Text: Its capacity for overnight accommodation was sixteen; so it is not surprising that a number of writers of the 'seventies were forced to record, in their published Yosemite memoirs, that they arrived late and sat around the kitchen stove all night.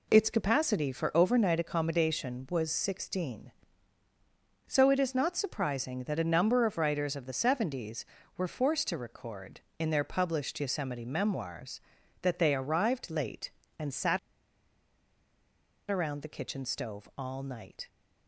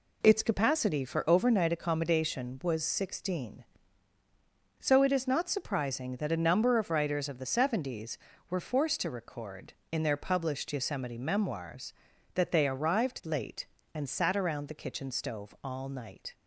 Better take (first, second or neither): second